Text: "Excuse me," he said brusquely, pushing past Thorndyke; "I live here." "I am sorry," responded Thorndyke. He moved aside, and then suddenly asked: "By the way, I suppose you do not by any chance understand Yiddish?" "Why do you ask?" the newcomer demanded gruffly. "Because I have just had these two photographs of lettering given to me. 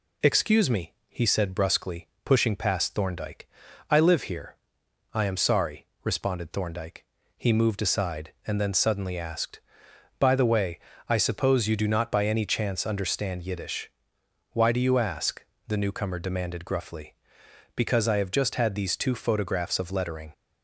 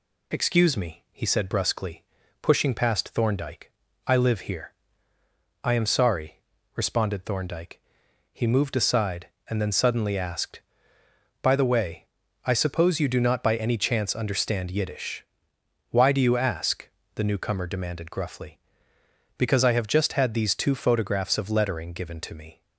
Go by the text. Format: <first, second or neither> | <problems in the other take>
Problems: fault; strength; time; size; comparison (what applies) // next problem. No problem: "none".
second | stops before "given to me"; at 20.3 s